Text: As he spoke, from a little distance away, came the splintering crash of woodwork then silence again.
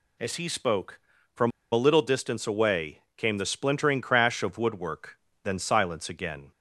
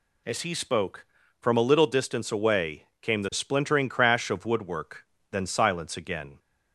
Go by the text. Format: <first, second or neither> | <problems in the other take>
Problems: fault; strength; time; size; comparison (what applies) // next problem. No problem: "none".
second | pauses between "from" and "a"; slight; at 1.5 s; 0.22 s long // pauses between "woodwork" and "then"; slight; at 5.1 s; 0.28 s long; slight in the second